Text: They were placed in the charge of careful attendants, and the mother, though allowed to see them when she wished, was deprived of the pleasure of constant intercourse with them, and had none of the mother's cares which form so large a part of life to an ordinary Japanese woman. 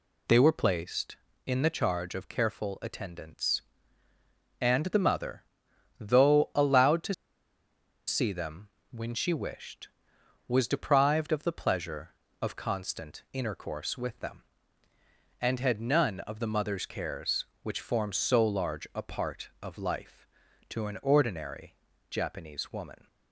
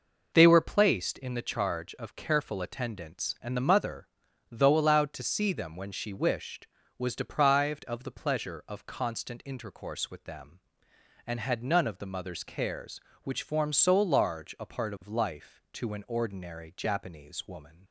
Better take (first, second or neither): second